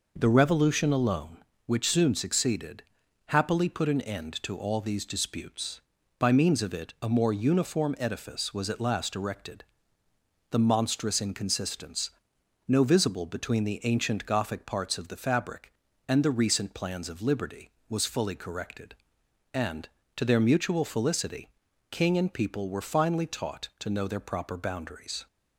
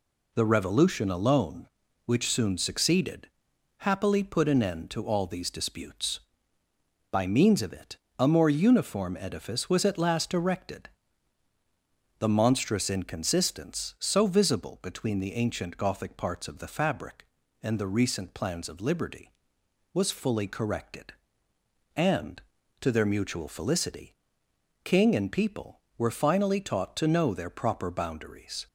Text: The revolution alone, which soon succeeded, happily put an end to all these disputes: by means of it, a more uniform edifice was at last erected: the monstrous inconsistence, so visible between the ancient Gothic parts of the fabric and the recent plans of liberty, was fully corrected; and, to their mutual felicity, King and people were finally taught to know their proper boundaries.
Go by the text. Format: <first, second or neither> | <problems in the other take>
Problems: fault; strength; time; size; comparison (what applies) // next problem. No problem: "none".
second | says "no" for "so"; at 12.6 s